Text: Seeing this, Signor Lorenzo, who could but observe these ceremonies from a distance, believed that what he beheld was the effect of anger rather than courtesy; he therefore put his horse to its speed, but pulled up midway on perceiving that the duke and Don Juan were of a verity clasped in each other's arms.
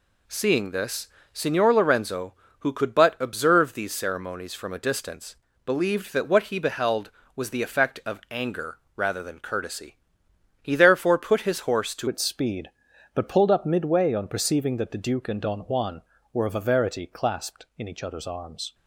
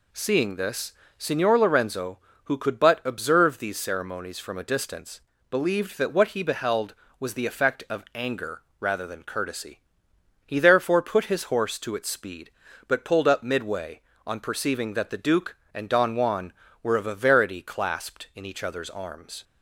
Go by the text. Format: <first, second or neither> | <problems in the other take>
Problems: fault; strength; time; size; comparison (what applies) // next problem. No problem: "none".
second | pauses between "anger" and "rather"; slight; at 8.7 s; 0.18 s long; slight in the second // changes voice at "its"; from 12.0 s on; 6.7 s long